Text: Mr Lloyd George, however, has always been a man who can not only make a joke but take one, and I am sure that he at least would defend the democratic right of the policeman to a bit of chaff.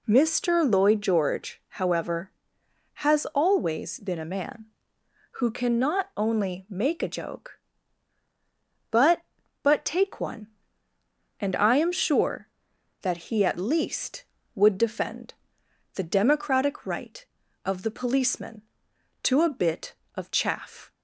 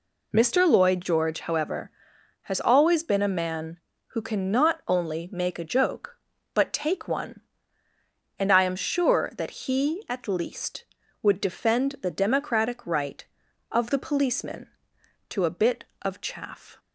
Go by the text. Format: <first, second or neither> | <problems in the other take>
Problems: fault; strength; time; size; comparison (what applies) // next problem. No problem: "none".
second | says "but" twice; at 9.6 s // pauses between "defend" and "the"; noticeable; at 15.3 s; 0.60 s long